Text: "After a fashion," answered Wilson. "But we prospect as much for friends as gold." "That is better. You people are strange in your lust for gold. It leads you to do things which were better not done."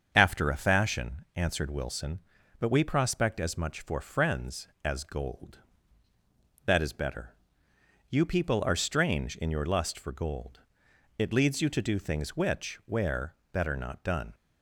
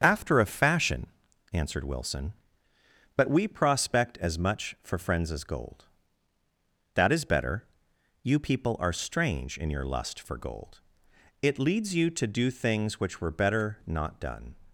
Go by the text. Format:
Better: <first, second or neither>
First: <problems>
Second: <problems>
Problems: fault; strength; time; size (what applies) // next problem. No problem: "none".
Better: second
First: starts louder than the rest; strong; until 1.1 s; 7 dB // says "where" for "were"; at 12.8 s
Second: starts louder than the rest; strong; until 1.0 s; 7 dB